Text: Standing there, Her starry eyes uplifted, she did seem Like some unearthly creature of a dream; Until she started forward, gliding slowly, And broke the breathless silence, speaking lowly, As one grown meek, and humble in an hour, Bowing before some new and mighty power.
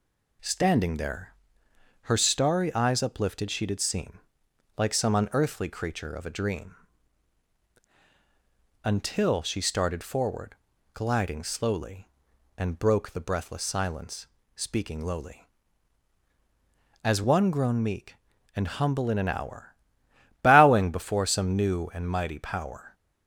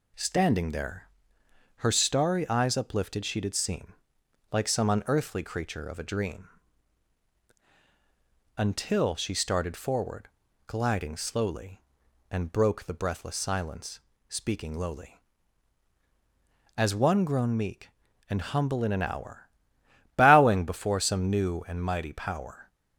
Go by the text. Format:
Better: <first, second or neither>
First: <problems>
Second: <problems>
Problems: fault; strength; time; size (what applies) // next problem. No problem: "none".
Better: neither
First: pauses between "seem" and "Like"; noticeable; at 4.1 s; 0.58 s long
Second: pauses between "seem" and "Like"; noticeable; at 3.9 s; 0.58 s long